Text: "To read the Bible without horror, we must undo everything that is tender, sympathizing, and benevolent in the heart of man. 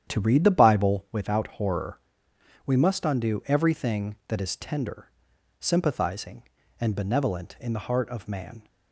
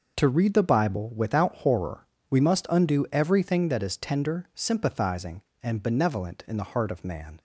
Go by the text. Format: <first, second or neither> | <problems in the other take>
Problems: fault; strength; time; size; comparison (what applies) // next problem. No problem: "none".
second | starts louder than the rest; strong; until 1.2 s; 9.5 dB